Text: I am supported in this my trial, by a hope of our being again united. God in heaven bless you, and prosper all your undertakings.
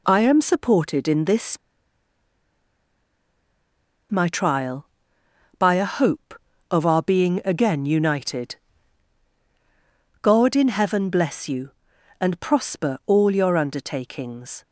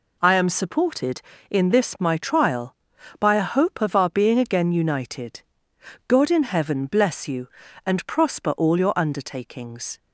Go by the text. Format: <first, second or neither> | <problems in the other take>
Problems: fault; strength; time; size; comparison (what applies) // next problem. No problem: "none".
second | pauses between "this" and "my"; strong; at 1.5 s; 2.5 s long